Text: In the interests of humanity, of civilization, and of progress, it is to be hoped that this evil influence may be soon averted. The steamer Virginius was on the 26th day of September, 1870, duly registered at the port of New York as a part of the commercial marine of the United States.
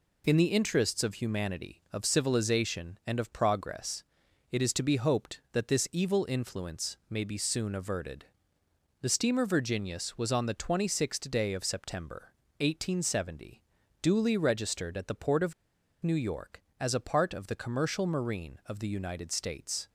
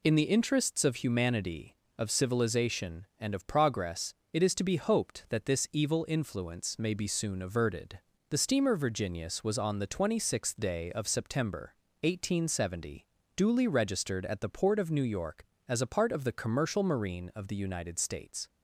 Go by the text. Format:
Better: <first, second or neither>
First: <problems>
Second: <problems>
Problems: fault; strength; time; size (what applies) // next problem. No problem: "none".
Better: second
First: pauses between "of" and "New"; noticeable; at 15.5 s; 0.48 s long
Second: none